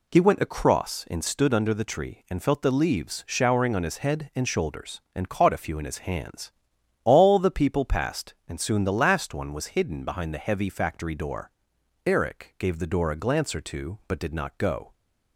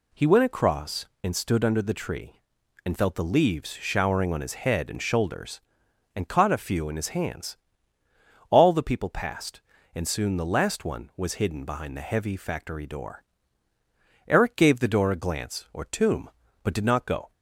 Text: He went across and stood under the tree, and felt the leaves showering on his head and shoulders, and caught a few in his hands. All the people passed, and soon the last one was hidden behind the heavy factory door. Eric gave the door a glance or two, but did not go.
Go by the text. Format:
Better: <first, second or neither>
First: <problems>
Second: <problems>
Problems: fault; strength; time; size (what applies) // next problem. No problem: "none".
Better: first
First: none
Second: says "tomb" for "two"; at 15.8 s